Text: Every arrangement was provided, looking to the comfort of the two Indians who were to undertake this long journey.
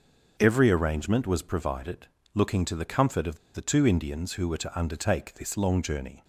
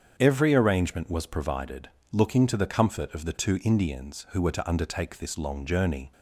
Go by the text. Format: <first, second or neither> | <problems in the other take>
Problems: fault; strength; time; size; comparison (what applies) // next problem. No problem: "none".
second | starts louder than the rest; until 1.4 s; 7 dB; strong in the second // pauses between "of" and "the"; slight; at 3.3 s; 0.16 s long